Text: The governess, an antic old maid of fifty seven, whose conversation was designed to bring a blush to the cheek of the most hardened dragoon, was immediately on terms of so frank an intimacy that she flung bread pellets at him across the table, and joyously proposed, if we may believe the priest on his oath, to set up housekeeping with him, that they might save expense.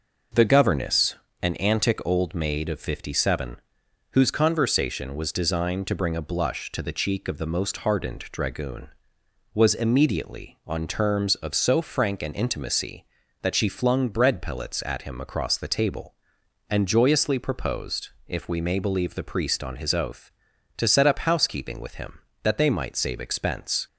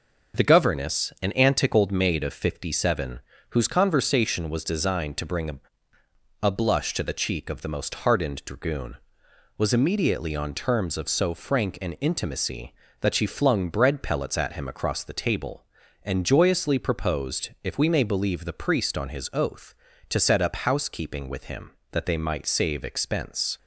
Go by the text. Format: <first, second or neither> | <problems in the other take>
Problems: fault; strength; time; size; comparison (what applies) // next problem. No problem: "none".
first | says "a" twice; at 6.4 s